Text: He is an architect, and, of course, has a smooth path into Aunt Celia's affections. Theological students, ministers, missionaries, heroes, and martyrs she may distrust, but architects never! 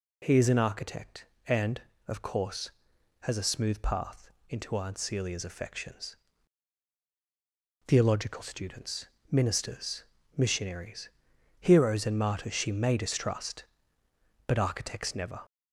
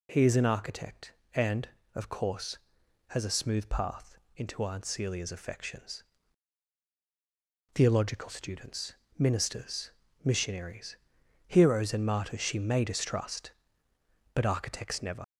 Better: first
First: pauses between "path" and "into"; slight; at 4.2 s; 0.18 s long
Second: pauses between "path" and "into"; slight; at 4.1 s; 0.18 s long // leaves "never" unfinished; at 15.2 s; 75 ms

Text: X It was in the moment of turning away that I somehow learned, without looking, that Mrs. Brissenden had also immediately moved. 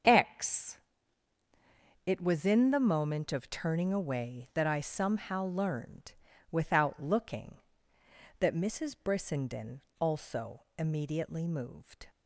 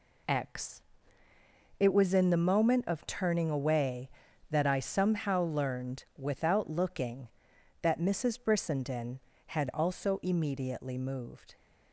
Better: second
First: starts louder than the rest; until 2.3 s; 7 dB // pauses between "X" and "It"; strong; at 0.7 s; 1.2 s long // skips "had"; at 9.8 s // pauses between "also" and "immediately"; slight; at 10.6 s; 0.16 s long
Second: pauses between "X" and "It"; noticeable; at 0.8 s; 0.98 s long

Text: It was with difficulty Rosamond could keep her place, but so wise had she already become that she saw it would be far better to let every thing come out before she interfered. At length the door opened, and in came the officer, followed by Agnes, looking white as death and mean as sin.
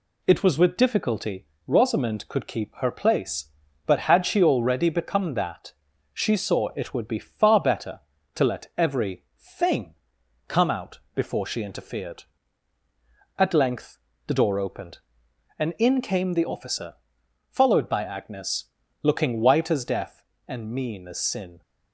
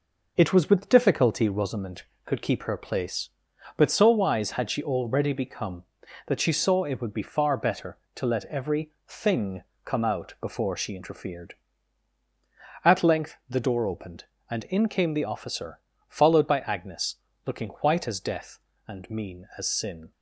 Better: second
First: pauses between "difficulty" and "Rosamond"; slight; at 1.4 s; 0.20 s long // skips "so wise"; at 4.0 s // pauses between "that" and "she"; at 5.7 s; 0.42 s long // pauses between "every" and "thing"; slight; at 9.2 s; 0.18 s long // pauses between "thing" and "come"; noticeable; at 9.9 s; 0.52 s long // pauses between "out" and "before"; slight; at 10.9 s; 0.16 s long // pauses between "length" and "the"; slight; at 13.9 s; 0.30 s long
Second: pauses between "every" and "thing"; slight; at 8.9 s; 0.16 s long // pauses between "thing" and "come"; slight; at 9.6 s; 0.20 s long

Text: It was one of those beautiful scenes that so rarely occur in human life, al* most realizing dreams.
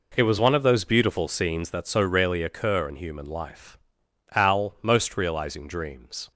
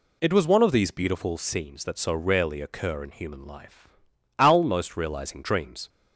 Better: first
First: none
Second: says "these" for "those"; at 0.7 s

